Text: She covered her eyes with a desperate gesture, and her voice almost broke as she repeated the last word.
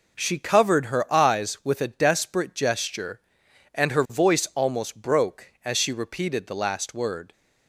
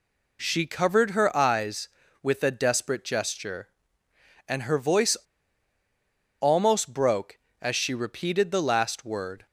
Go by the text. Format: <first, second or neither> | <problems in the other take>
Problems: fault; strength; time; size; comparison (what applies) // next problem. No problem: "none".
first | pauses between "voice" and "almost"; strong; at 5.1 s; 1.2 s long